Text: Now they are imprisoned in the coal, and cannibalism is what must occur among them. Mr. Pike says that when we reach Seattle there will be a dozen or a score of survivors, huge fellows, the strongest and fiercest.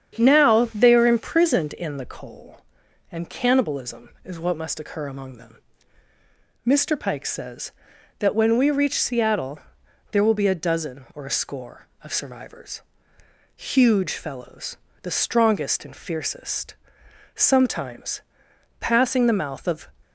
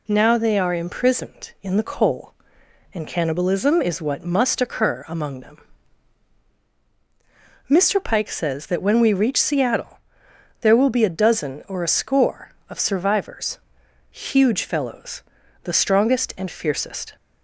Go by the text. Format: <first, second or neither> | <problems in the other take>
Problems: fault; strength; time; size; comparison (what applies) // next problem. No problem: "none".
second | starts louder than the rest; strong; until 1.2 s; 8.5 dB // pauses between "Seattle" and "there"; noticeable; at 9.5 s; 0.52 s long; noticeable in the second // goes on to say "Sometimes passing the mouth of"; strong; from 17.3 s on; 2.5 s long